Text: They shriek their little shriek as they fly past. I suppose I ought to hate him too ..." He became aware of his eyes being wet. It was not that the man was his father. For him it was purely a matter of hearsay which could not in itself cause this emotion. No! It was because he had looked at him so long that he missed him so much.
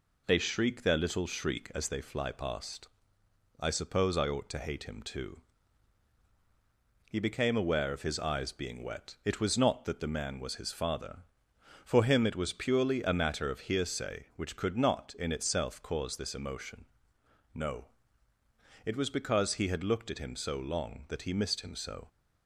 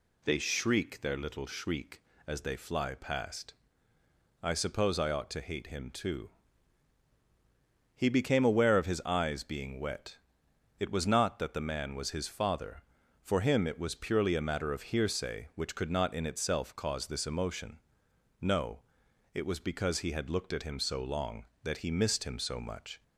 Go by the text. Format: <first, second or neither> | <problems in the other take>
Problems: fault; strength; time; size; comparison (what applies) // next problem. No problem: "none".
second | stops before "much"; at 22.0 s